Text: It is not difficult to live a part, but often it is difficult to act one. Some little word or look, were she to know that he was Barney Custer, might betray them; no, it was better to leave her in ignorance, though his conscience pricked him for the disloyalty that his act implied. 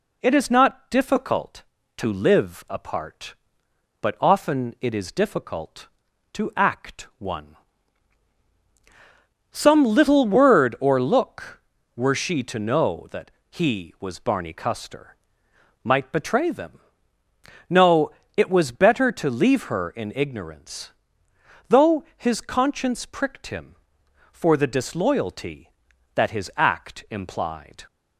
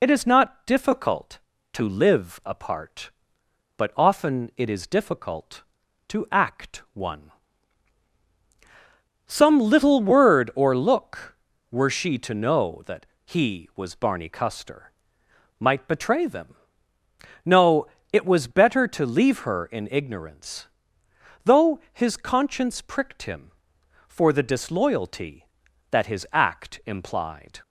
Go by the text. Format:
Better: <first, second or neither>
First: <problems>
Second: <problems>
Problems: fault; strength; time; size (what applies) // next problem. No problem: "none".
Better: first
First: pauses between "that" and "he"; slight; at 13.3 s; 0.20 s long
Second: loses the start of "It"; at 0.0 s; 35 ms // pauses between "that" and "he"; slight; at 13.0 s; 0.20 s long